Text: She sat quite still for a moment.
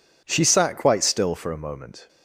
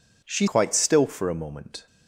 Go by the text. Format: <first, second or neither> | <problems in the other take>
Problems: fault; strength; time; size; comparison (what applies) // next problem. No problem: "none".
first | skips "sat"; at 0.4 s